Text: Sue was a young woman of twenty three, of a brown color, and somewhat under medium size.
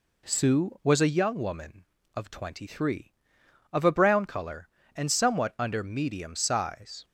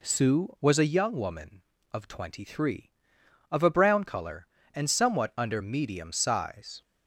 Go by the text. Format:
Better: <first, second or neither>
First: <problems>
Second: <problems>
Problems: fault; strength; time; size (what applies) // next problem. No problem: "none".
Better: neither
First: none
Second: none